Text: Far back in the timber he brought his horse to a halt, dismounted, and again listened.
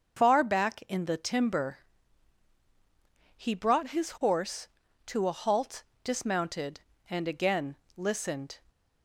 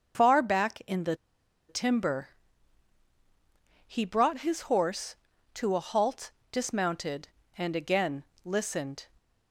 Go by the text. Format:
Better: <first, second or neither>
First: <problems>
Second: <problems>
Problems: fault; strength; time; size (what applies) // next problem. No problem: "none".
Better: first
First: starts louder than the rest; until 1.2 s; 6 dB // pauses between "timber" and "he"; strong; at 1.7 s; 1.5 s long // pauses between "again" and "listened"; slight; at 7.7 s; 0.22 s long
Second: starts louder than the rest; until 1.7 s; 6.5 dB // pauses between "the" and "timber"; noticeable; at 1.1 s; 0.54 s long // pauses between "timber" and "he"; strong; at 2.2 s; 1.5 s long // pauses between "again" and "listened"; slight; at 8.2 s; 0.22 s long